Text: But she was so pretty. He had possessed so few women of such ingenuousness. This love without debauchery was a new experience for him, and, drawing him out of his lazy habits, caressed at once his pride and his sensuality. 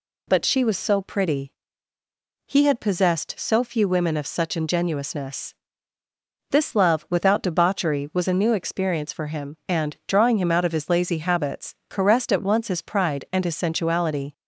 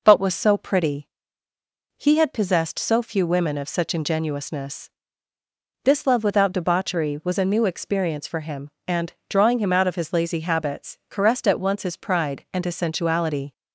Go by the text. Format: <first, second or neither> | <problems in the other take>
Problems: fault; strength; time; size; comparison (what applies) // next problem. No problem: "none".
first | skips "she"; at 0.2 s